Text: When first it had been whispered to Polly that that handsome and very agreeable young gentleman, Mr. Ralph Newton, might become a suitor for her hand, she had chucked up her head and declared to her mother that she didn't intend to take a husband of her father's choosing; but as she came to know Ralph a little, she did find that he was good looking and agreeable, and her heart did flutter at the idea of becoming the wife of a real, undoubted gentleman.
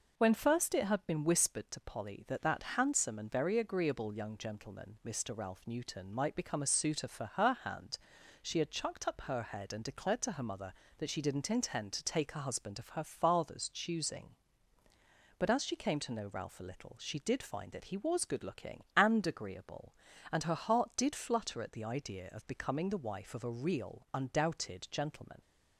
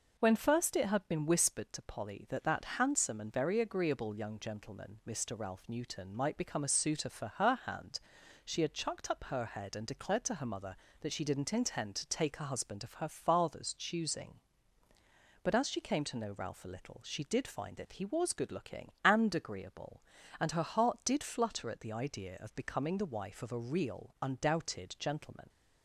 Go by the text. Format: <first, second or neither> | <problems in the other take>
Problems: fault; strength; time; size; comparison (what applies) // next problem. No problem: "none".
neither | none